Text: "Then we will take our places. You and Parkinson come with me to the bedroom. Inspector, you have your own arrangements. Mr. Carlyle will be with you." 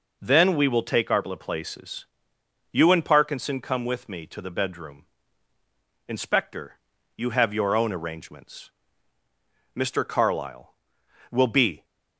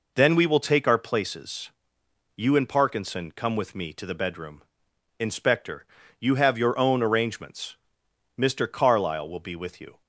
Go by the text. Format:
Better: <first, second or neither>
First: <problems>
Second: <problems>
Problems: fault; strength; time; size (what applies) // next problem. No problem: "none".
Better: second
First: stops before "with you"; at 11.8 s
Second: none